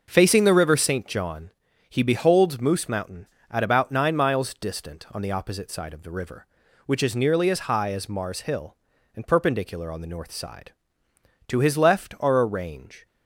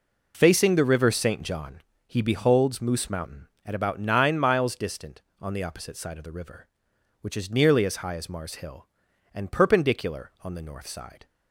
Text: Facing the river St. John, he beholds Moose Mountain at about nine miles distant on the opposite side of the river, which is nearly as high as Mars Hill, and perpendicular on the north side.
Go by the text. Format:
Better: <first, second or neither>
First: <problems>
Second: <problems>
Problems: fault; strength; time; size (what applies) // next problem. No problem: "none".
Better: second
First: goes on to say "To his left are a range"; from 11.4 s on; 1.5 s long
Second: none